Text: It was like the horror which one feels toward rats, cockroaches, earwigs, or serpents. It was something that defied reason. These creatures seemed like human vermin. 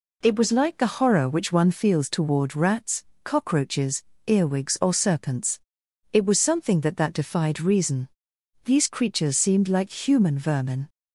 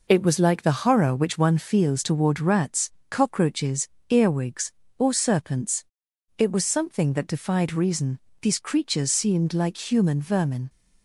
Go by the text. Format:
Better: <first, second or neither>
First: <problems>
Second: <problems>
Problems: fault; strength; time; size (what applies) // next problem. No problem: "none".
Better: second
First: says "that" twice; at 6.9 s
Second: none